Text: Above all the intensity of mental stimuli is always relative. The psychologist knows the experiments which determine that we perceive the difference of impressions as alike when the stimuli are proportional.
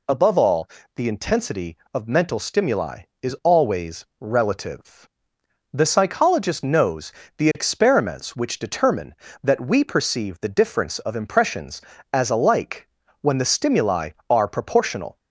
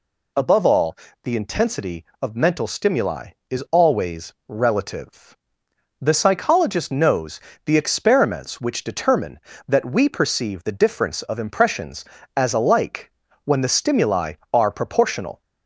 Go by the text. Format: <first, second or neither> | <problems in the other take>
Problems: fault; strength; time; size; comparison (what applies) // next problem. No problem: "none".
neither | pauses between "all" and "the"; slight; the same in both // pauses between "knows" and "the"; slight; the same in both // pauses between "alike" and "when"; slight; the same in both